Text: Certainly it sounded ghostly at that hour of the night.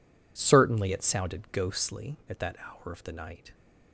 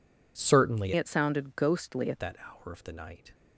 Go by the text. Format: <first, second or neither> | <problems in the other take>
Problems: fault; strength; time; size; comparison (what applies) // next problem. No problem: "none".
first | changes voice from "it" to "at"; from 0.9 to 2.1 s; 1.2 s long